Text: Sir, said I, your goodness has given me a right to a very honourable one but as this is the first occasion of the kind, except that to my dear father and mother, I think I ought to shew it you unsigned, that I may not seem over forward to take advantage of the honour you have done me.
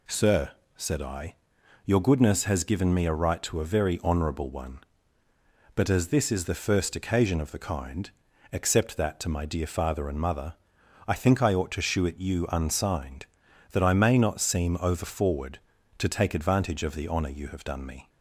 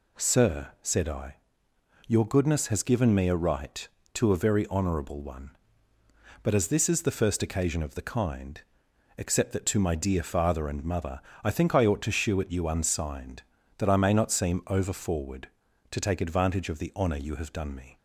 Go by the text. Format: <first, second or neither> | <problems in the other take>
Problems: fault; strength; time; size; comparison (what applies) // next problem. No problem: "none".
neither | none